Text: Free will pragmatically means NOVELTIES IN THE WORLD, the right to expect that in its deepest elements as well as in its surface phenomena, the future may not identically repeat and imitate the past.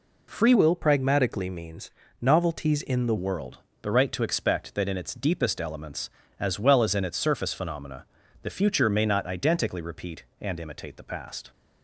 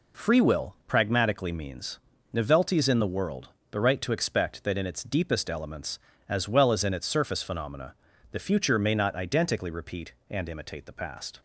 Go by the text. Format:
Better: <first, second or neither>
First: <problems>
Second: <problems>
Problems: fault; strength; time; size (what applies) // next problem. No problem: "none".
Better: second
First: changes voice from "will" to "THE"; from 0.5 to 3.1 s; 2.6 s long // pauses between "means" and "NOVELTIES"; slight; at 1.8 s; 0.32 s long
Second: pauses between "means" and "NOVELTIES"; slight; at 1.9 s; 0.32 s long